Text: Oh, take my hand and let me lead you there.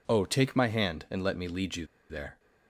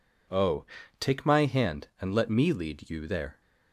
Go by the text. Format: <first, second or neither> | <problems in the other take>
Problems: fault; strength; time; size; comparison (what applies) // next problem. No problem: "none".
second | pauses between "you" and "there"; slight; at 1.8 s; 0.25 s long